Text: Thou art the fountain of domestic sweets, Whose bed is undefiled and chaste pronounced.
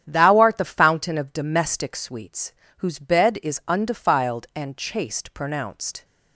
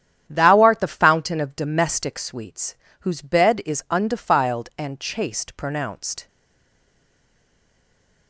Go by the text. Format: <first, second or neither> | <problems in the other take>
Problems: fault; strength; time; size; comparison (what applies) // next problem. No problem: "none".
first | starts louder than the rest; strong; until 1.2 s; 10 dB; strong in the first // stays silent after the last word; noticeable; from 6.2 s on; 2.0 s long